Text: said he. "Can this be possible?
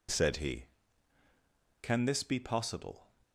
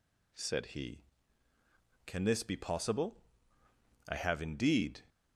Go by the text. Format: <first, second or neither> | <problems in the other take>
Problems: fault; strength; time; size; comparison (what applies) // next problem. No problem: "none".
first | goes on to say "I have indeed"; noticeable; from 4.0 s on; 0.96 s long